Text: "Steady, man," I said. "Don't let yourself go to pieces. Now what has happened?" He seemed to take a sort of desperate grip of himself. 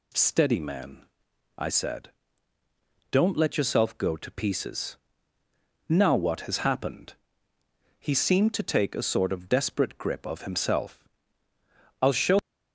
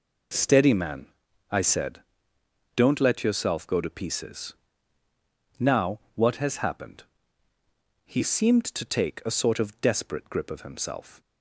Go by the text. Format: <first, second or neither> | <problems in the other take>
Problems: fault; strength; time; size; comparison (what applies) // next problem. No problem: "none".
second | goes on to say "I'll show"; slight; from 12.0 s on; 0.36 s long